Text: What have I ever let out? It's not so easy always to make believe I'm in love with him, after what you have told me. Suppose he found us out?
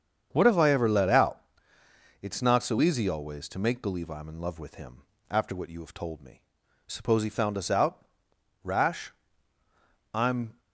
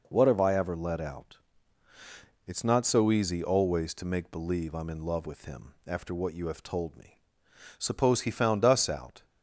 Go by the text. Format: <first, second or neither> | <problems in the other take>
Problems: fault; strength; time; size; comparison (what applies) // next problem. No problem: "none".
second | starts louder than the rest; strong; until 1.3 s; 7.5 dB // goes on to say "Rash I'm"; strong; from 8.6 s on; 1.9 s long